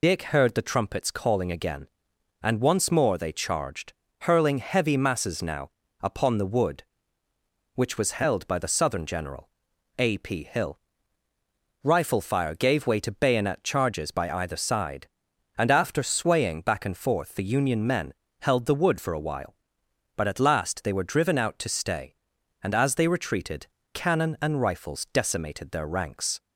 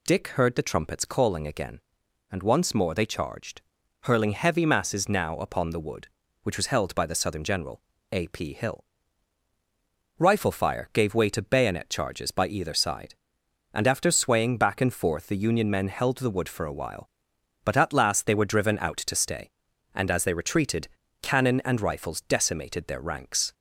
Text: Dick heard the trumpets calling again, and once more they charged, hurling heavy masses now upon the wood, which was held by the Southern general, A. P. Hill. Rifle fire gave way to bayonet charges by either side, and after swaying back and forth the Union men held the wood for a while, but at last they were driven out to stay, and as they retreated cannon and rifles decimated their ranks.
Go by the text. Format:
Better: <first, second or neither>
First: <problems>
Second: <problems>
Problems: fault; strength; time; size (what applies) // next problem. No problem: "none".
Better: second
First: loses the start of "Dick"; at 0.0 s; 35 ms // pauses between "now" and "upon"; slight; at 5.6 s; 0.32 s long // pauses between "men" and "held"; slight; at 18.1 s; 0.26 s long // pauses between "retreated" and "cannon"; slight; at 23.6 s; 0.24 s long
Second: pauses between "retreated" and "cannon"; slight; at 20.8 s; 0.34 s long